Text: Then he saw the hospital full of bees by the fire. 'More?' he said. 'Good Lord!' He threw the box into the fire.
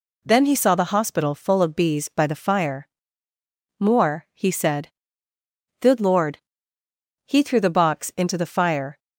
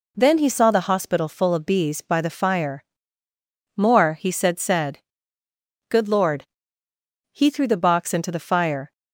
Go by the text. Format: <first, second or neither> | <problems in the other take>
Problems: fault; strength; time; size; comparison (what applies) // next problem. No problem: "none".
first | says "said" twice; at 4.5 s